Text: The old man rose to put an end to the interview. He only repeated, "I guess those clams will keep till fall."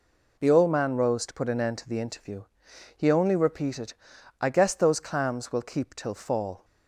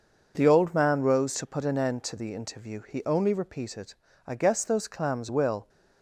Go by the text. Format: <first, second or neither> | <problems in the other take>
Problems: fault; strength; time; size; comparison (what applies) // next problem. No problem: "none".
first | stops before "keep till fall"; at 5.6 s